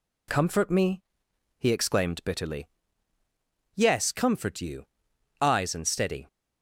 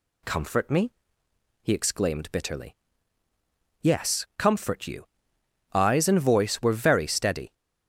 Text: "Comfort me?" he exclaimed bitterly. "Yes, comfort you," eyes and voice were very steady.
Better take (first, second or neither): second